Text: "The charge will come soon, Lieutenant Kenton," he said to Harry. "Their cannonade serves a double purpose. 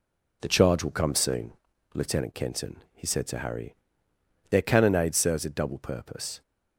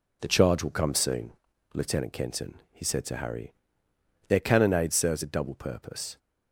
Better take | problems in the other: neither | none

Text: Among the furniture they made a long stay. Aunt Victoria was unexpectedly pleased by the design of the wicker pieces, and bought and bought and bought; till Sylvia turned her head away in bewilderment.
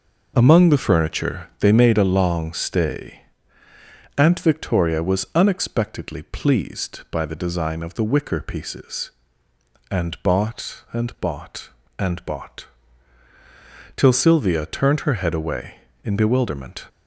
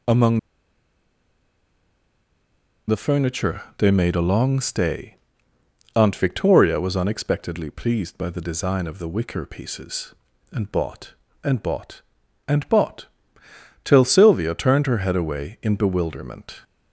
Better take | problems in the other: first | pauses between "Among" and "the"; strong; at 0.3 s; 2.4 s long // pauses between "furniture" and "they"; slight; at 3.6 s; 0.16 s long

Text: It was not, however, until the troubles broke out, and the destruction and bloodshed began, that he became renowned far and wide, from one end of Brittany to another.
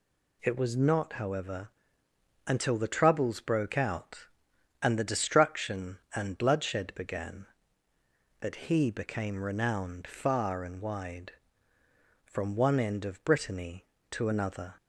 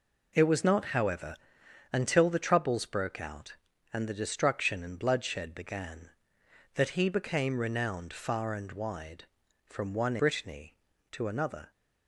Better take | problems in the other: first | skips "end of"; at 10.1 s

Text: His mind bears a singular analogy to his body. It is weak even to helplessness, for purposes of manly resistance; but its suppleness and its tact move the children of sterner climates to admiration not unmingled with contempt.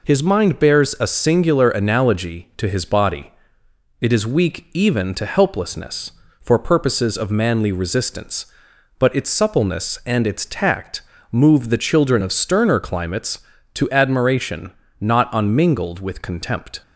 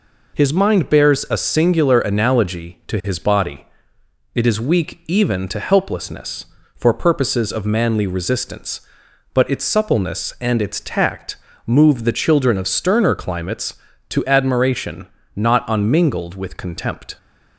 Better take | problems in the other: neither | pauses between "tact" and "move"; slight; the same in both // pauses between "admiration" and "not"; slight; the same in both

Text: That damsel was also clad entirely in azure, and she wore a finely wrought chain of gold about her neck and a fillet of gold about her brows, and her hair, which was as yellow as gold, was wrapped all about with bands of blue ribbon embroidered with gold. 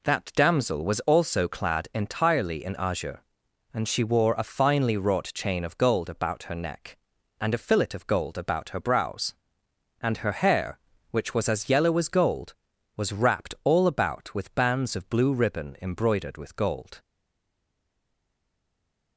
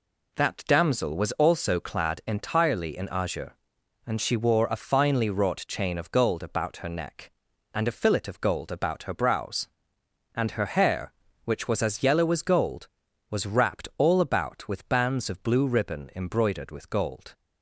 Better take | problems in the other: second | stays silent after the last word; from 16.9 s on; 2.2 s long

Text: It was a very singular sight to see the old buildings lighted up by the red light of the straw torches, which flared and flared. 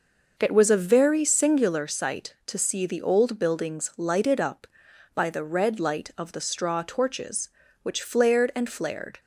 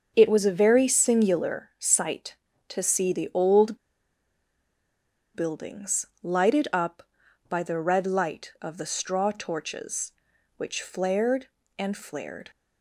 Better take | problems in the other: first | starts louder than the rest; until 1.1 s; 6.5 dB // pauses between "old" and "buildings"; strong; at 3.7 s; 1.5 s long // pauses between "buildings" and "lighted"; slight; at 6.0 s; 0.16 s long

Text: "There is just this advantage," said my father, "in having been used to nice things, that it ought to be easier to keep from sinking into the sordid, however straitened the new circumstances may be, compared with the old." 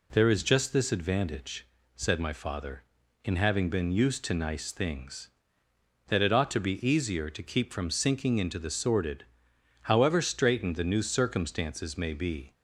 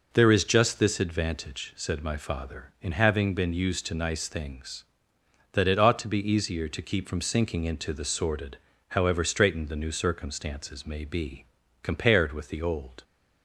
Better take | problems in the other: second | stops before "compared with the old"; at 12.5 s

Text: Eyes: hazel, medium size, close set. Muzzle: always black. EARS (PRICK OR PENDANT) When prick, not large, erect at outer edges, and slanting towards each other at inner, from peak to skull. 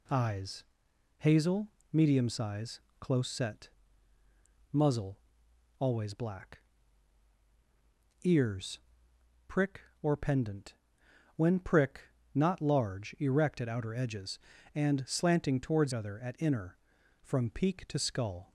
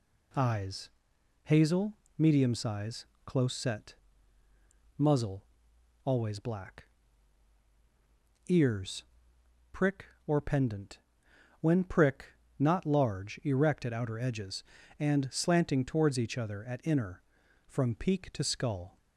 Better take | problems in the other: second | skips "each"; at 15.9 s

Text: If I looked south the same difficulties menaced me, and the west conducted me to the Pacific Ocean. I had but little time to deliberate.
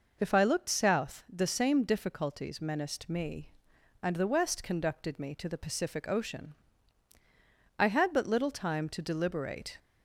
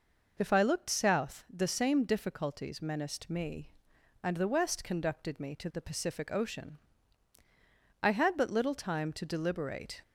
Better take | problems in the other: neither | none

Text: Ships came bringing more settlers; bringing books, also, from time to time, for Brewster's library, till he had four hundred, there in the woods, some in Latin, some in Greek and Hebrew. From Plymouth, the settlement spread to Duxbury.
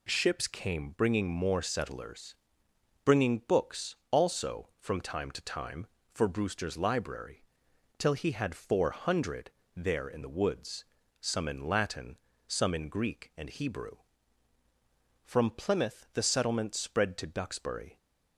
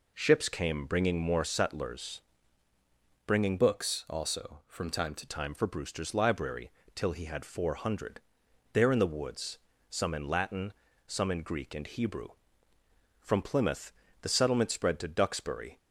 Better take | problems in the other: first | changes voice from "books" to "to"; from 3.5 to 5.2 s; 1.7 s long

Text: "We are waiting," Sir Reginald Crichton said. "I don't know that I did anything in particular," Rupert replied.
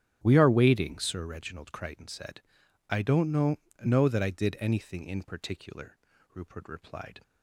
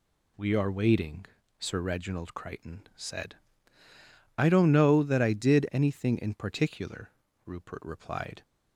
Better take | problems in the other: second | starts louder than the rest; strong; until 1.2 s; 10.5 dB // says "know" twice; at 3.8 s

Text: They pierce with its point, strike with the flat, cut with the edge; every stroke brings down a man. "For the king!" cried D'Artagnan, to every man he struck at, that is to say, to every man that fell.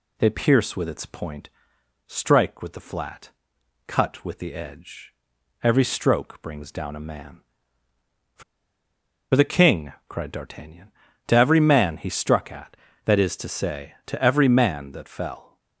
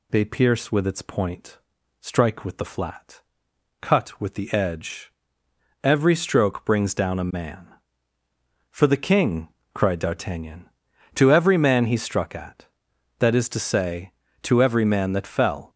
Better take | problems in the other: second | pauses between "For" and "the"; noticeable; at 8.4 s; 0.91 s long

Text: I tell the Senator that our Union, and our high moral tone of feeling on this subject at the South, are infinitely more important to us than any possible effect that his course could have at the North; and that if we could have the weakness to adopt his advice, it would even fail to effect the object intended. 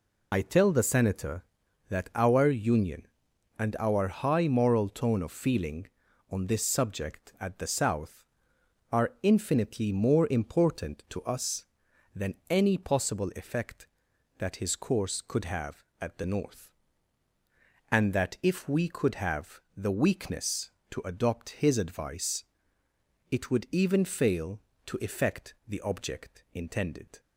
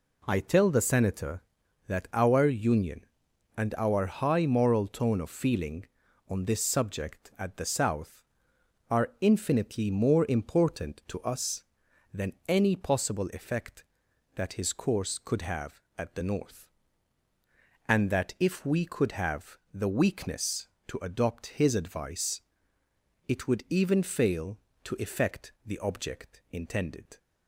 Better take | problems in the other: second | loses the start of "I"; at 0.3 s; 70 ms // pauses between "than" and "any"; slight; at 12.3 s; 0.16 s long; slight in the second // pauses between "have" and "the"; slight; at 19.6 s; 0.16 s long; slight in the second // pauses between "effect" and "the"; slight; at 25.5 s; 0.16 s long; slight in the second

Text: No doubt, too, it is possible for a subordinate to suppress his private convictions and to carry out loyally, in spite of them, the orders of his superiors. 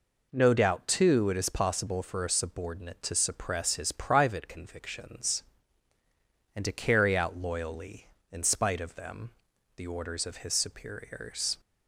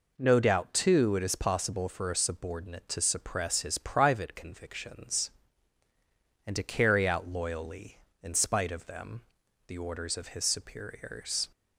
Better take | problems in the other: neither | none

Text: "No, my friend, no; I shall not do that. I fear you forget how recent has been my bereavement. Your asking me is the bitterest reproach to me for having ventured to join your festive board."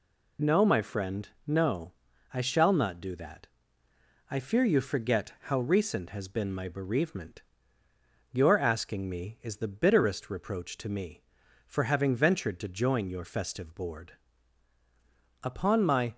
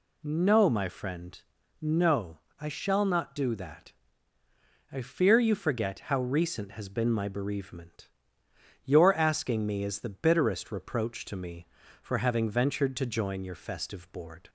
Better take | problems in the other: second | goes on to say "Upon my"; noticeable; from 15.4 s on; 0.72 s long

